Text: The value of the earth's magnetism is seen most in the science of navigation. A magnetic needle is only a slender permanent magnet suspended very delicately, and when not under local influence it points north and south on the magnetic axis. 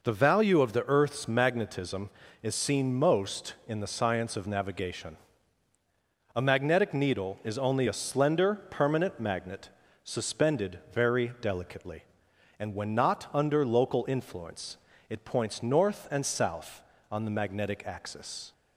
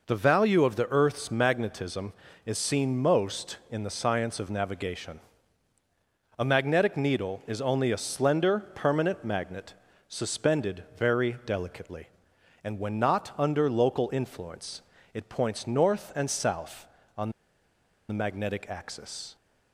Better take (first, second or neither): first